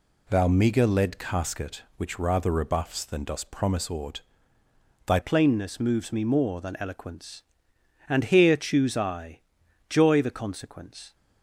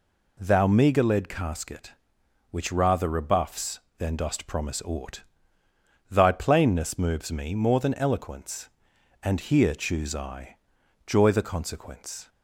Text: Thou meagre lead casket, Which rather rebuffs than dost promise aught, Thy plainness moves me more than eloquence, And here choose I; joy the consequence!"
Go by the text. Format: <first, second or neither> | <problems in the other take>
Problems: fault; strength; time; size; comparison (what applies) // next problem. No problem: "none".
second | changes voice at "plainness"; from 5.2 s on; 5.9 s long